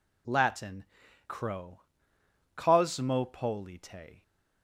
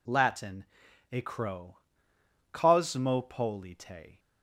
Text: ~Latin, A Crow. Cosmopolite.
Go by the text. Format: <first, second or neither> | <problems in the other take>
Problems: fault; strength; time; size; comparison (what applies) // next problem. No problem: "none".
second | skips "A"; at 1.0 s